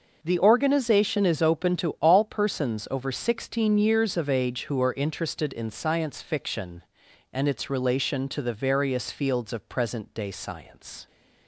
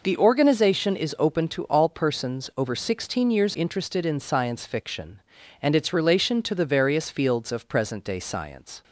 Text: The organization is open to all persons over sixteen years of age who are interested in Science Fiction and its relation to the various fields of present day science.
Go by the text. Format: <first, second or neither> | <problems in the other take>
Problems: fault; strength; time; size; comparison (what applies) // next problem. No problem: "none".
first | skips "of age who are"; at 3.5 s